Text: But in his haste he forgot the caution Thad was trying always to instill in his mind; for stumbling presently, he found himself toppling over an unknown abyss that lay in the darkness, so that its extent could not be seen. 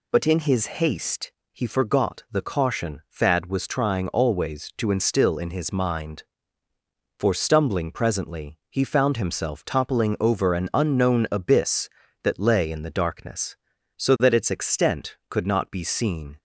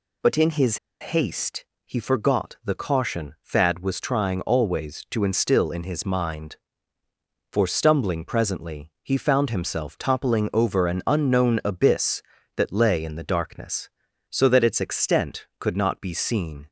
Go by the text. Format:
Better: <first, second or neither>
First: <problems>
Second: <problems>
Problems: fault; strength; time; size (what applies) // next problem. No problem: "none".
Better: first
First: pauses between "haste" and "he"; slight; at 1.3 s; 0.20 s long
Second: pauses between "his" and "haste"; slight; at 0.7 s; 0.24 s long // pauses between "haste" and "he"; slight; at 1.6 s; 0.20 s long